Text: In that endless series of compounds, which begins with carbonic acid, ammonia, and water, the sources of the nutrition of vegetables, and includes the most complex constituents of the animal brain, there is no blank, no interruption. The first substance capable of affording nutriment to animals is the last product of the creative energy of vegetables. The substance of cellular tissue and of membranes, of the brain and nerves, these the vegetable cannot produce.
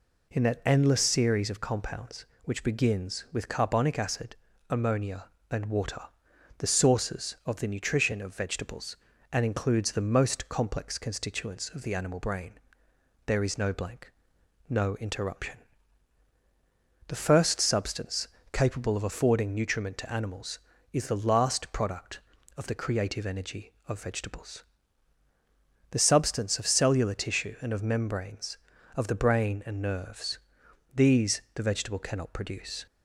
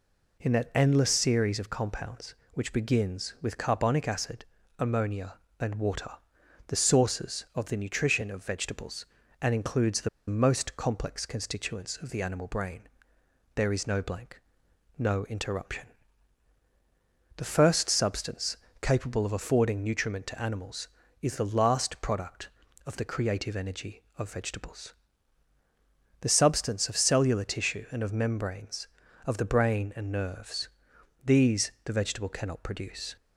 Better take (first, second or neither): first